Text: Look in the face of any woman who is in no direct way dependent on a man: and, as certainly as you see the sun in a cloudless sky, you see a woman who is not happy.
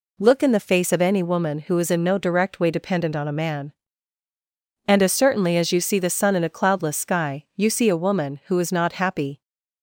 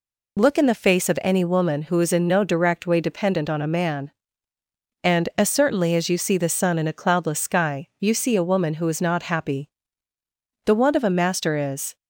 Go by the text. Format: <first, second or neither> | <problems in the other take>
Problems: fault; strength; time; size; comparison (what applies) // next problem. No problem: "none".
first | goes on to say "The want of a master is"; noticeable; from 10.6 s on; 1.3 s long